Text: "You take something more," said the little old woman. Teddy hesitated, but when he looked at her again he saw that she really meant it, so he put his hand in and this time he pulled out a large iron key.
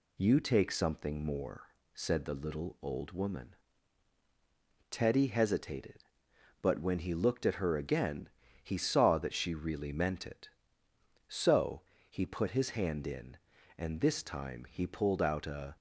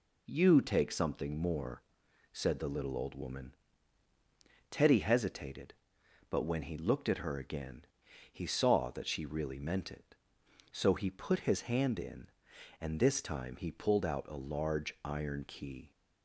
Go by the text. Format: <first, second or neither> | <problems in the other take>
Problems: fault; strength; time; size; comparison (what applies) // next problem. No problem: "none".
second | pauses between "again" and "he"; slight; at 8.2 s; 0.36 s long; noticeable in the second // pauses between "so" and "he"; slight; at 11.8 s; 0.28 s long // stops before "large iron key"; at 15.7 s